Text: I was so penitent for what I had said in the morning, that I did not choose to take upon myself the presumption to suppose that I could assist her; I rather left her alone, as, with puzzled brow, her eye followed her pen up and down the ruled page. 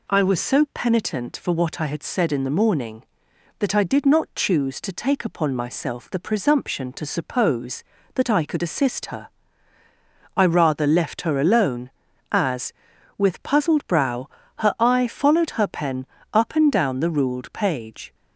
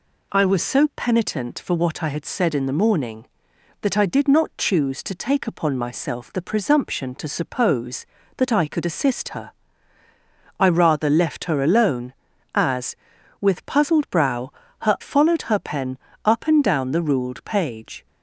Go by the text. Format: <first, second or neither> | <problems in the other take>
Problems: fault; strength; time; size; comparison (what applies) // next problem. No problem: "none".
first | skips "eye"; at 14.9 s // pauses between "pen" and "up"; slight; at 15.9 s; 0.26 s long; slight in the first